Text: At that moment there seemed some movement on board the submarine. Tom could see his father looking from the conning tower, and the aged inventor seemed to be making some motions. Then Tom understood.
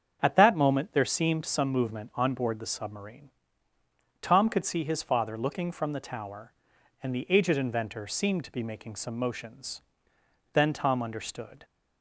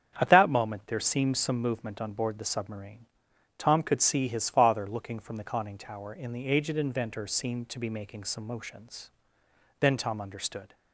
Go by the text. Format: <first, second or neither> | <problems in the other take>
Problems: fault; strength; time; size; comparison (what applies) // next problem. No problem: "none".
second | starts louder than the rest; strong; until 1.2 s; 7.5 dB; strong in the second // skips "conning"; at 6.0 s